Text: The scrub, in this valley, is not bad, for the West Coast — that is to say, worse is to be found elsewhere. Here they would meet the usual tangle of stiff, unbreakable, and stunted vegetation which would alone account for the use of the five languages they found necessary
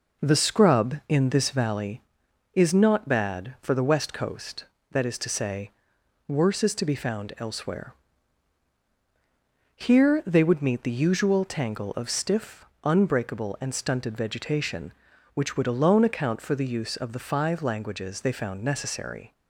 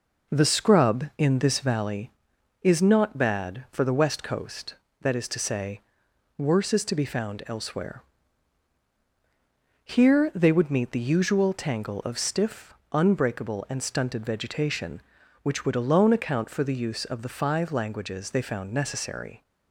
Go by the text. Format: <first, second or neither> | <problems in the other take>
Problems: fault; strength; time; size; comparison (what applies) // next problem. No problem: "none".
neither | none